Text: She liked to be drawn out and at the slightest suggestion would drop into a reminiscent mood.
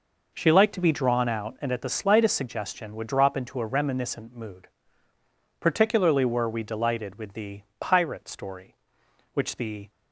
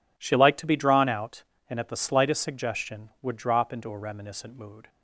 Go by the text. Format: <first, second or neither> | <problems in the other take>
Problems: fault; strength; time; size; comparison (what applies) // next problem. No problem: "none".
second | goes on to say "Particularly were we delighted with the Pirate Story which the"; strong; from 5.5 s on; 4.3 s long